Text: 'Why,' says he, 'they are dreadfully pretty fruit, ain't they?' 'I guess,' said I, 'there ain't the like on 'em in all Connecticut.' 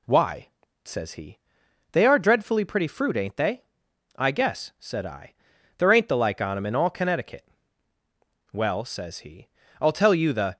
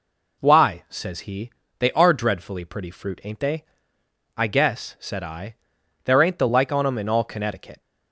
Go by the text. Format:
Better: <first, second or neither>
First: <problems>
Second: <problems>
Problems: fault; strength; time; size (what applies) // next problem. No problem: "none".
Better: second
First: goes on to say "Well says he I'll tell you the"; strong; from 8.5 s on; 2.0 s long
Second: none